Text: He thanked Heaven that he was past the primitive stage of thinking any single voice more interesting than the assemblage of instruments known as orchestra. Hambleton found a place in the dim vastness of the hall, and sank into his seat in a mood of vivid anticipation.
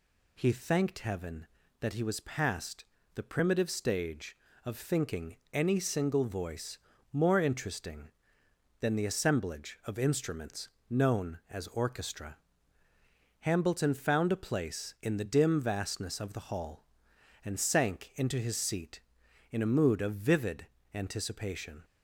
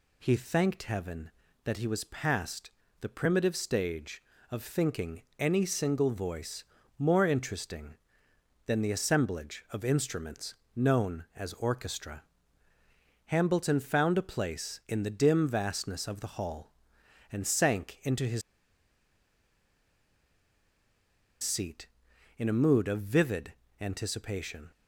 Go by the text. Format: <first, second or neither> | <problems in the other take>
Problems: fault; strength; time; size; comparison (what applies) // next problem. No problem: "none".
first | pauses between "past" and "the"; slight; at 2.6 s; 0.30 s long; slight in the first // pauses between "thinking" and "any"; slight; at 5.2 s; 0.16 s long; slight in the first // pauses between "voice" and "more"; slight; at 6.6 s; 0.36 s long; slight in the first // pauses between "instruments" and "known"; slight; at 10.5 s; 0.22 s long; slight in the first // pauses between "his" and "seat"; strong; at 18.4 s; 3.0 s long // pauses between "vivid" and "anticipation"; slight; at 23.5 s; 0.26 s long; slight in the first